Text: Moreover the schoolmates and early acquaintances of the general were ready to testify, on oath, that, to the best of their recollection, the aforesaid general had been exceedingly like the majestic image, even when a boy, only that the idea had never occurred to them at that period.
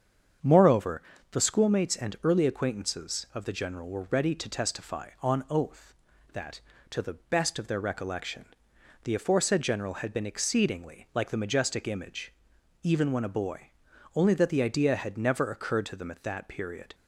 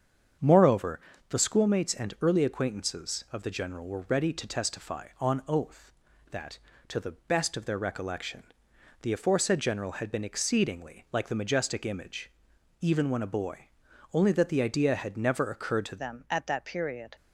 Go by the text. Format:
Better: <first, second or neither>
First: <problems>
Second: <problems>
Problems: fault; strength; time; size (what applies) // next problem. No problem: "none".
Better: first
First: starts louder than the rest; strong; until 1.7 s; 7.5 dB // pauses between "Moreover" and "the"; slight; at 1.0 s; 0.30 s long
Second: starts louder than the rest; strong; until 1.7 s; 7.5 dB // pauses between "Moreover" and "the"; slight; at 0.9 s; 0.30 s long // changes voice at "them"; from 15.9 s on; 1.2 s long